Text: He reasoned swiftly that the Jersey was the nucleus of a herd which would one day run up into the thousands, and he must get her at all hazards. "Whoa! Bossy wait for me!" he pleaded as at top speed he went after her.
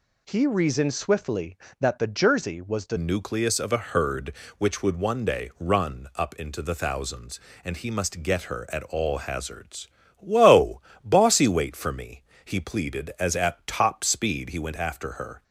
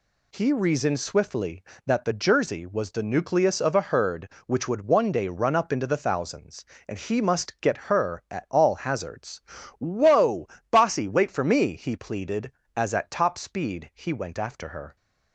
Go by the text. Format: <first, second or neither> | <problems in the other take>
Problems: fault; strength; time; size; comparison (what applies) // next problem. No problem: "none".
second | changes voice at "nucleus"; from 2.9 s on; 12.5 s long